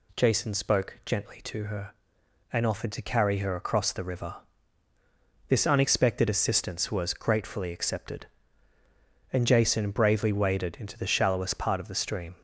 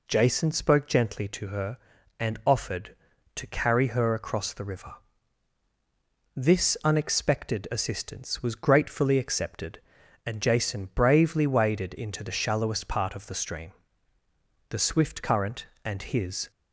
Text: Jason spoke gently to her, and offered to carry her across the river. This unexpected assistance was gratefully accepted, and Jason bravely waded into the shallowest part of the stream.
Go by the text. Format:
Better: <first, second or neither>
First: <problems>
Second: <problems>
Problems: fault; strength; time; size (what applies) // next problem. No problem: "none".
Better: first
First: none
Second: goes on to say "The swift current and his"; strong; from 14.7 s on; 1.8 s long